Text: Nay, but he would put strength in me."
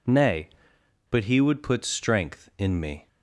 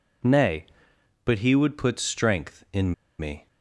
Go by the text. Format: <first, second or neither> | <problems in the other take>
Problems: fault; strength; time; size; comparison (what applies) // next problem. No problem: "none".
first | pauses between "in" and "me"; slight; at 2.9 s; 0.26 s long